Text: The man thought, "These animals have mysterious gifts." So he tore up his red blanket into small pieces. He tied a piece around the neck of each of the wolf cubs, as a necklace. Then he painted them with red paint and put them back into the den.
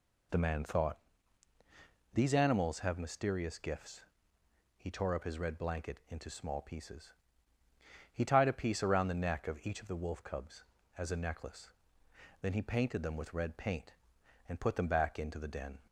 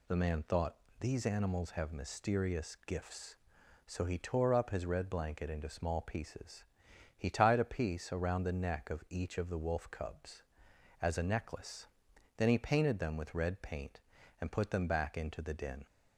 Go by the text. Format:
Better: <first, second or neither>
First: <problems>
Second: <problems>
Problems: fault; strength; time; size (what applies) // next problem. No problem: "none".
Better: second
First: skips "So"; at 4.4 s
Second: none